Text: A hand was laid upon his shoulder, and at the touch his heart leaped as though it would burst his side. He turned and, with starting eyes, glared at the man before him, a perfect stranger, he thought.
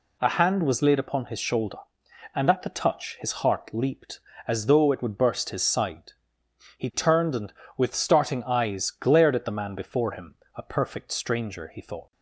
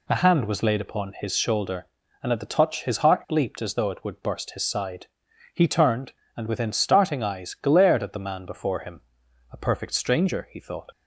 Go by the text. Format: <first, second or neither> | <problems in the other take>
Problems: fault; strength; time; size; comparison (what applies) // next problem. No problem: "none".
first | says "within" for "with"; at 6.4 s